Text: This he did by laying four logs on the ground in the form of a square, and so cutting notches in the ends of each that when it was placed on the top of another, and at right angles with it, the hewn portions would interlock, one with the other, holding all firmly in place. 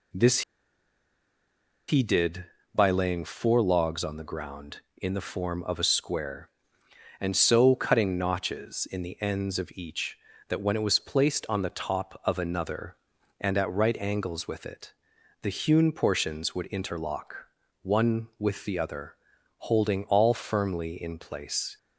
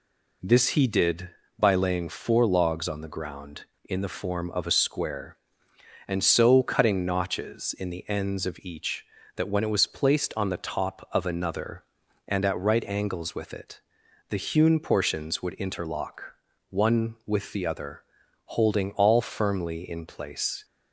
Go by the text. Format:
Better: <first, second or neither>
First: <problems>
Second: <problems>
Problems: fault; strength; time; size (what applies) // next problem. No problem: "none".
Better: second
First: pauses between "This" and "he"; strong; at 0.4 s; 1.4 s long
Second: none